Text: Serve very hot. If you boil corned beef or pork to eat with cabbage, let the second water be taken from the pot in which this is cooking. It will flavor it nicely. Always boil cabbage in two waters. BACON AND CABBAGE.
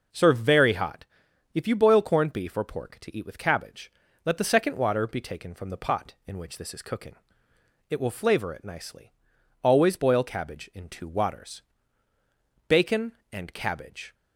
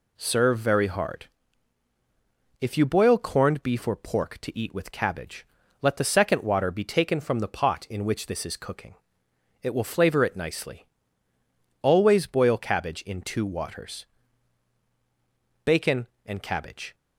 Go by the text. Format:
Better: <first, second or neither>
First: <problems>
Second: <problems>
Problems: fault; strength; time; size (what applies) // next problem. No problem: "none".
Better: first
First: none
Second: says "hard" for "hot"; at 0.8 s